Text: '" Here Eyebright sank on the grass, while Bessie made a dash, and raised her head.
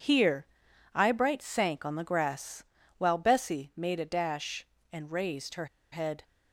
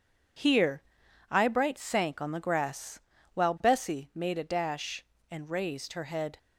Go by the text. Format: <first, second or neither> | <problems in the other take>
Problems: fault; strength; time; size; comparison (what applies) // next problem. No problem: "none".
second | pauses between "Here" and "Eyebright"; noticeable; at 0.4 s; 0.48 s long; noticeable in the second // pauses between "her" and "head"; slight; at 5.6 s; 0.26 s long